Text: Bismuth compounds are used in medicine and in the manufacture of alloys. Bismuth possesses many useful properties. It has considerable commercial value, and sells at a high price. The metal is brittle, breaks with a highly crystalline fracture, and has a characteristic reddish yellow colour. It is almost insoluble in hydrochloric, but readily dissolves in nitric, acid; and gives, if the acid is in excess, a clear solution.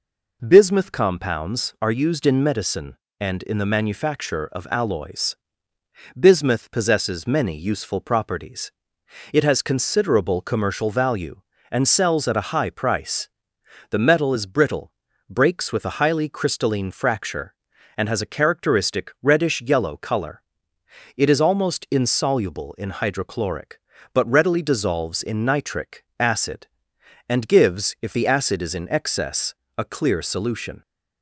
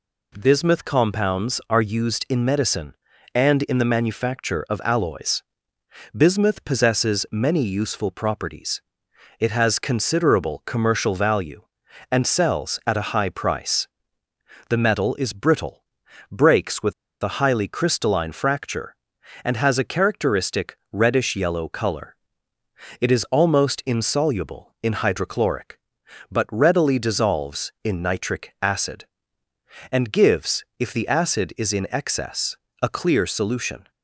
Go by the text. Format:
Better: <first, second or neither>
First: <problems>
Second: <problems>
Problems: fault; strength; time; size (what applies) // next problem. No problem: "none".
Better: first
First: none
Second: pauses between "with" and "a"; slight; at 16.9 s; 0.30 s long // pauses between "characteristic" and "reddish"; slight; at 20.7 s; 0.16 s long